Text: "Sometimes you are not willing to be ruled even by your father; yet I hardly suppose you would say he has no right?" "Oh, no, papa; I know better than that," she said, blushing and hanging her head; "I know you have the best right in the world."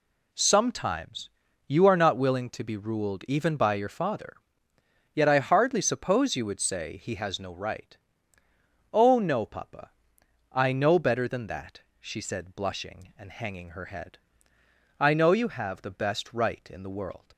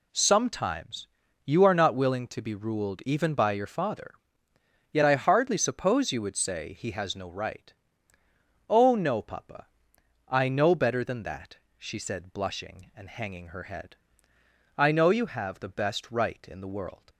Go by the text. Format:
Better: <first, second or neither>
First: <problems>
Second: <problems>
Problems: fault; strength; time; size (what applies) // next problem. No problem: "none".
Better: neither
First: pauses between "Sometimes" and "you"; at 1.2 s; 0.40 s long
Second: pauses between "Sometimes" and "you"; at 1.0 s; 0.40 s long